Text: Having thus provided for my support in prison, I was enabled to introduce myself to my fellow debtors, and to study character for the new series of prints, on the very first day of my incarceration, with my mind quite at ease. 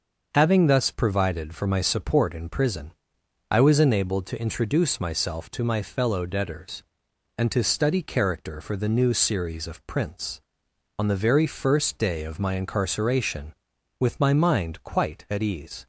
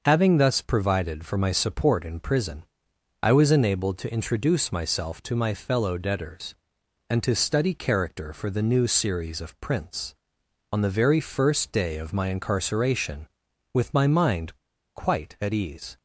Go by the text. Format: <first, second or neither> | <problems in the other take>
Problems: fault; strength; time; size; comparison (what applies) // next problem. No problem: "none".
first | starts louder than the rest; noticeable; until 1.0 s; 6 dB; noticeable in the first // pauses between "mind" and "quite"; at 14.5 s; 0.39 s long